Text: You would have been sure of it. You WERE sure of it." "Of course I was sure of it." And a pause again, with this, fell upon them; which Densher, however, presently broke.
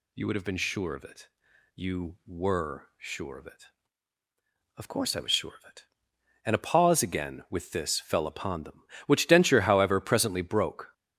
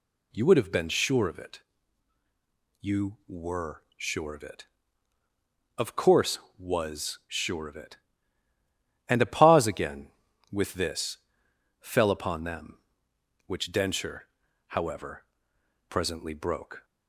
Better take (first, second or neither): first